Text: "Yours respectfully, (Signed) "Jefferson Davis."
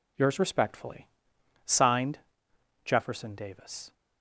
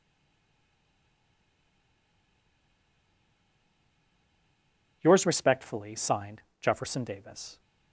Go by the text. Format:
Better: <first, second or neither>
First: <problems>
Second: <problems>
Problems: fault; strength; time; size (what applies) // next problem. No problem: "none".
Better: first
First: none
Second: stays silent before the first word; strong; until 5.0 s; 5.0 s long